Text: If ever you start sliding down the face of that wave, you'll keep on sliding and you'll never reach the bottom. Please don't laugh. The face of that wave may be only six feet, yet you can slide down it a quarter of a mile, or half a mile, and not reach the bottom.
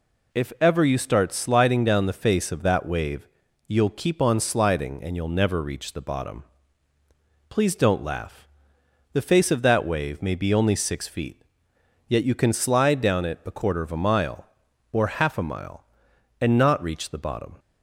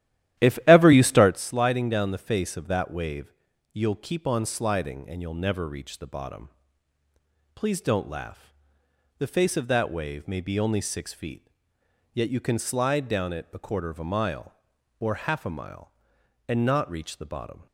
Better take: first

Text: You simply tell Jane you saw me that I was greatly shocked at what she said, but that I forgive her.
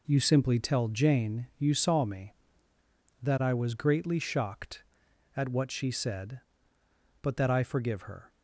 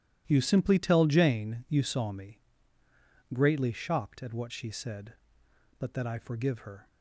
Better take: first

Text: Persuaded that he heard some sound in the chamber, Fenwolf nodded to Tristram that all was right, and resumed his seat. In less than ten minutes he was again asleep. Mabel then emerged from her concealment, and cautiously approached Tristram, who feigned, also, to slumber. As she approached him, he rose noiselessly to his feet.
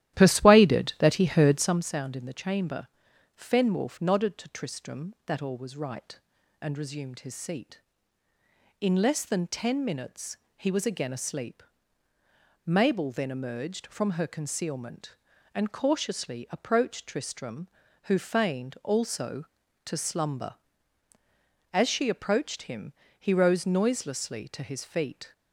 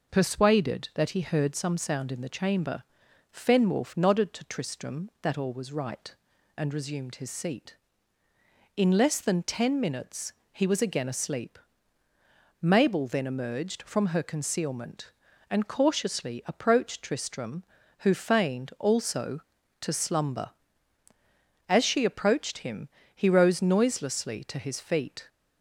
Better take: second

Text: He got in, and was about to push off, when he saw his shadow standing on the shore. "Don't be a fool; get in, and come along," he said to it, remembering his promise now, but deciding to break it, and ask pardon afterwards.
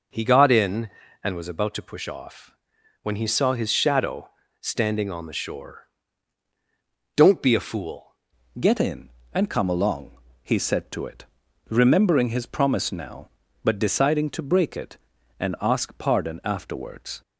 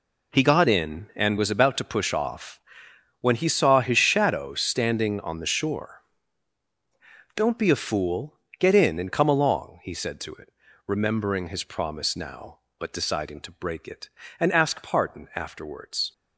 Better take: second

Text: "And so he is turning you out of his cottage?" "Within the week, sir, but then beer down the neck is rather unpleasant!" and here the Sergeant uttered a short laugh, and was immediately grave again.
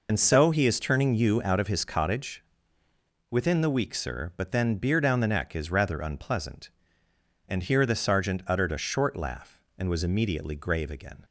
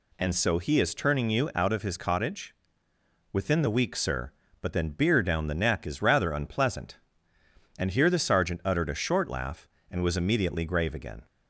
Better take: second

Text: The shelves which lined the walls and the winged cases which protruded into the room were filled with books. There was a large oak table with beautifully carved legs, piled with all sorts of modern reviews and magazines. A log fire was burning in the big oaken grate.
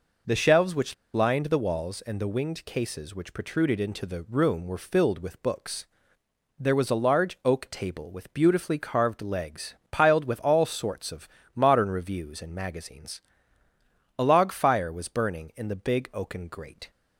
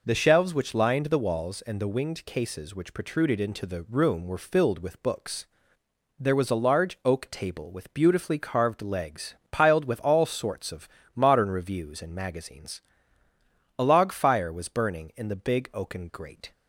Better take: second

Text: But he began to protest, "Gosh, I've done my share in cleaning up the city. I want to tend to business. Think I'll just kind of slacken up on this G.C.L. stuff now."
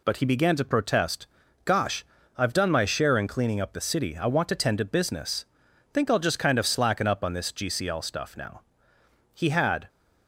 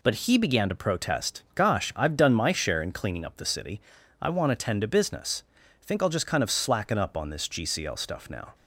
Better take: second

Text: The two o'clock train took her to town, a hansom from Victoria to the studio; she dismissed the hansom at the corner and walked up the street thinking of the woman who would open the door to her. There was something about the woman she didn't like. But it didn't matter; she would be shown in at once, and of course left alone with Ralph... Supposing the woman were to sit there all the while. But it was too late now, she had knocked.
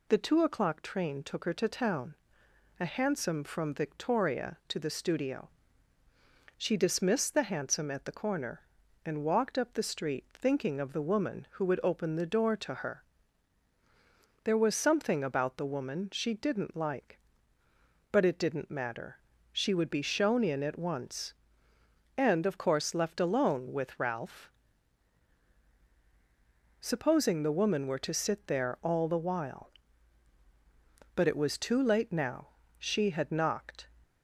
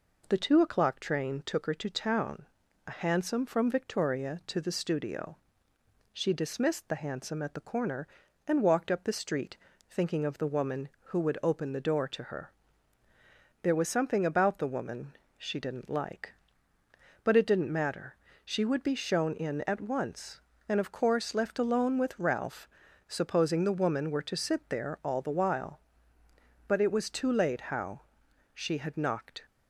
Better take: first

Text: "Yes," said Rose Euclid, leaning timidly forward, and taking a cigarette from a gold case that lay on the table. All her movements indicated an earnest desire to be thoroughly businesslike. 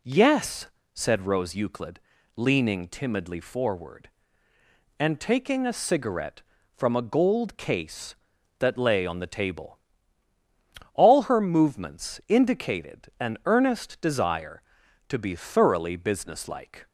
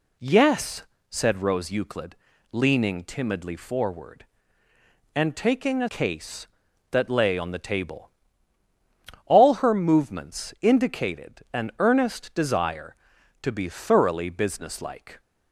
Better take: first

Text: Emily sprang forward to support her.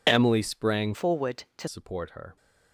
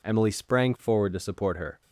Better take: second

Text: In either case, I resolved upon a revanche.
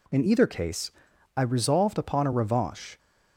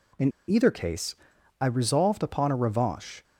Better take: first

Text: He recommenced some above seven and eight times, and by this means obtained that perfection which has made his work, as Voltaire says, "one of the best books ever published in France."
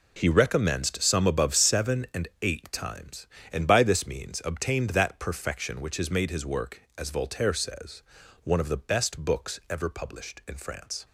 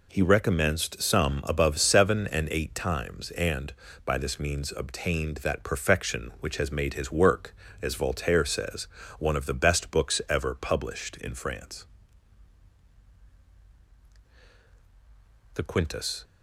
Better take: first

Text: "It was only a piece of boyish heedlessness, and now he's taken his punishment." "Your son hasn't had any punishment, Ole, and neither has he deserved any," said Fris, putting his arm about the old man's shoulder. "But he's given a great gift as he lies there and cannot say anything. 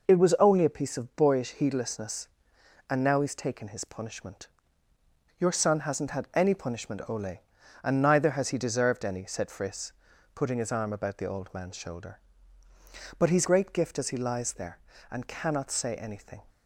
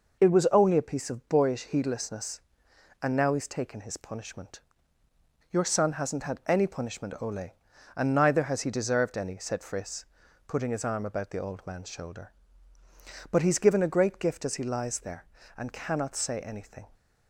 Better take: second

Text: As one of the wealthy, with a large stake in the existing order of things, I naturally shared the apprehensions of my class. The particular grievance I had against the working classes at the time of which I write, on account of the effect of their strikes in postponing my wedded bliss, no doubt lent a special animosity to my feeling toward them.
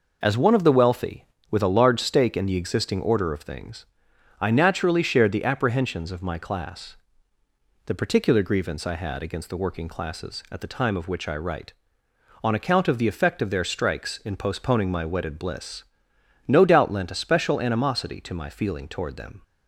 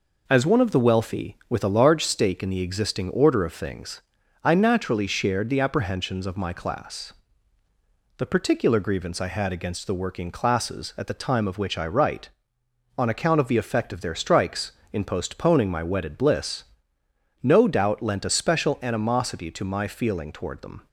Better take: neither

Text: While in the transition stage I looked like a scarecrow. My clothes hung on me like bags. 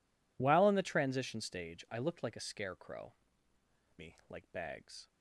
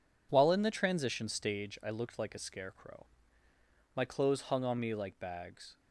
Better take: second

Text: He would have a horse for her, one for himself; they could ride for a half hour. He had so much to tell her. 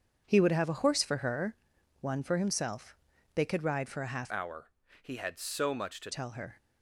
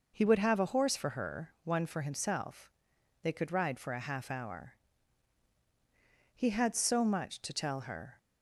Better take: second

